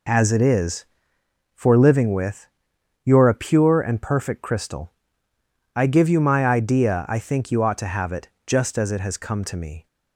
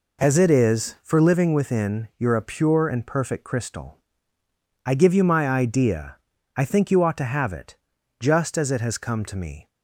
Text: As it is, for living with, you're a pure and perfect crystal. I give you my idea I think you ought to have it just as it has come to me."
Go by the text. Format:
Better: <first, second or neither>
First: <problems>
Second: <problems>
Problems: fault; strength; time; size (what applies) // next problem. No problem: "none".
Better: first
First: pauses between "it" and "just"; slight; at 8.2 s; 0.18 s long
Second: says "within" for "with"; at 1.5 s // pauses between "idea" and "I"; at 6.1 s; 0.40 s long // pauses between "it" and "just"; at 7.7 s; 0.42 s long